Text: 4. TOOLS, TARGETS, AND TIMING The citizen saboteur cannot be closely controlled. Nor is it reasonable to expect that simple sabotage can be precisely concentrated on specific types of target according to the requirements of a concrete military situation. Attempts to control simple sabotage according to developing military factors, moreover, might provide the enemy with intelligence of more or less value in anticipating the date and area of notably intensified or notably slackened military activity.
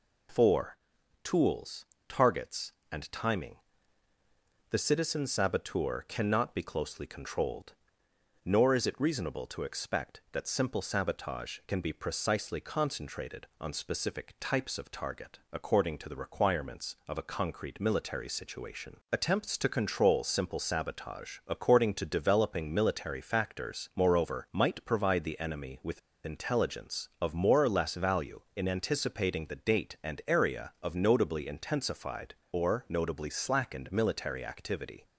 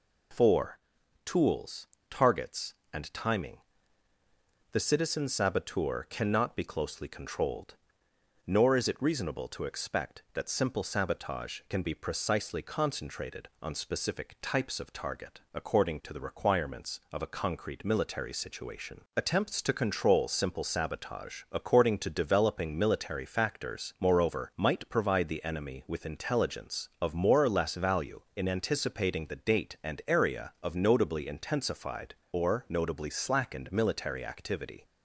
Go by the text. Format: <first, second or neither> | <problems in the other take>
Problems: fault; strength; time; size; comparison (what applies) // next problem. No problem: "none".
second | pauses between "TIMING" and "The"; at 3.5 s; 1.1 s long; also in the second // pauses between "with" and "intelligence"; slight; at 25.9 s; 0.26 s long